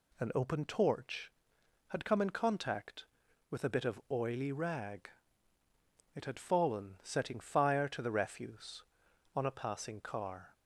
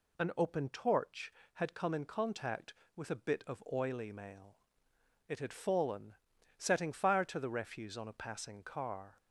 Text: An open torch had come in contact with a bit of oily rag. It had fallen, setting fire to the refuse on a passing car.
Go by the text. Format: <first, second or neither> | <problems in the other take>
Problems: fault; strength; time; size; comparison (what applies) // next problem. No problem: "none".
first | says "mail" for "rag"; at 4.1 s